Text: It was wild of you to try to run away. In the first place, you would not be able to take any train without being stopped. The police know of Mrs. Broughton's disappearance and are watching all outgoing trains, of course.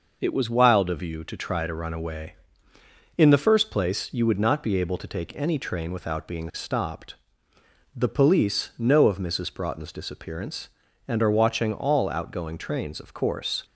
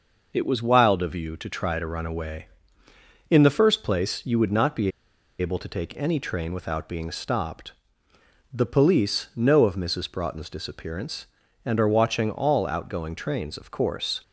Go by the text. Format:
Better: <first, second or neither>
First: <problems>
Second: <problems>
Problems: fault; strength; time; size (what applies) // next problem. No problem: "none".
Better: first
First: none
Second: pauses between "be" and "able"; noticeable; at 4.9 s; 0.49 s long